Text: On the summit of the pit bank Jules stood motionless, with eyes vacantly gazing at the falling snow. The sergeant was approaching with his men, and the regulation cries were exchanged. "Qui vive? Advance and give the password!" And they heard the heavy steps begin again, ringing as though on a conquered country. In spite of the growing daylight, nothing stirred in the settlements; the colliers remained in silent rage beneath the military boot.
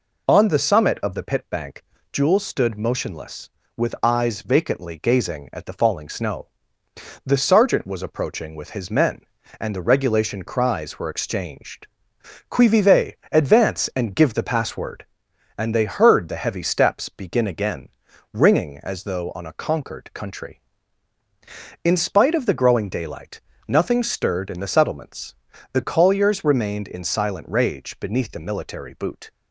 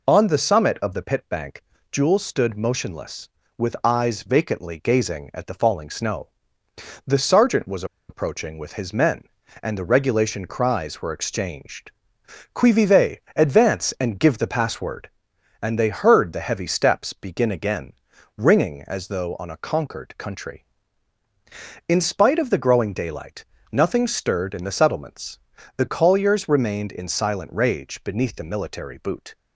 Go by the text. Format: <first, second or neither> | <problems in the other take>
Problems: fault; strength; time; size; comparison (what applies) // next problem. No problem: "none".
first | pauses between "bank" and "Jules"; slight; at 1.6 s; 0.30 s long; slight in the first // pauses between "was" and "approaching"; slight; at 7.8 s; 0.24 s long